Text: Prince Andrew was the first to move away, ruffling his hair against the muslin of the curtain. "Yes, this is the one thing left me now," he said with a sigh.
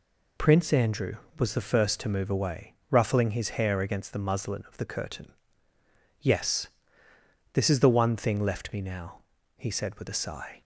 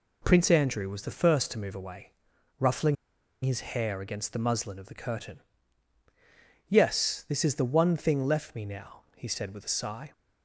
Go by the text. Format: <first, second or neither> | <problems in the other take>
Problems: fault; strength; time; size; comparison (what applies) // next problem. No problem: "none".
first | pauses between "ruffling" and "his"; noticeable; at 2.9 s; 0.47 s long